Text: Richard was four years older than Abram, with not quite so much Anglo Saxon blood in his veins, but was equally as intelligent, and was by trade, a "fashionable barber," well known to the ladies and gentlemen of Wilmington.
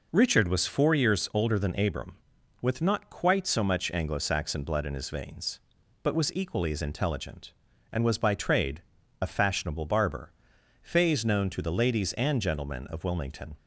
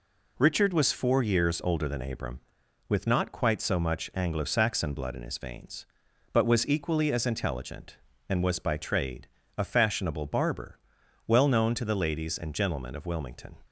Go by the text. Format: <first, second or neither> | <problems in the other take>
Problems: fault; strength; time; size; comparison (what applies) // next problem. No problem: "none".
second | says "phase" for "well"; at 10.8 s